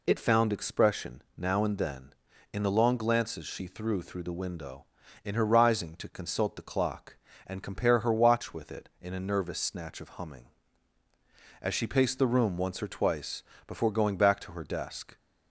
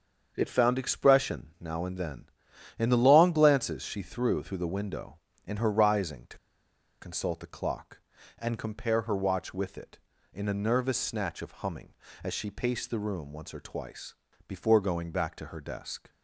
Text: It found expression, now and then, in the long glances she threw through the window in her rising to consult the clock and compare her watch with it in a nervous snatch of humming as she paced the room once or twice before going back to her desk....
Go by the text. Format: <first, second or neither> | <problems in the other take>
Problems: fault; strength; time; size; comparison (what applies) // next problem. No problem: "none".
first | starts louder than the rest; until 1.3 s; 7 dB // pauses between "to" and "consult"; noticeable; at 6.3 s; 0.60 s long // pauses between "twice" and "before"; slight; at 14.1 s; 0.32 s long; slight in the first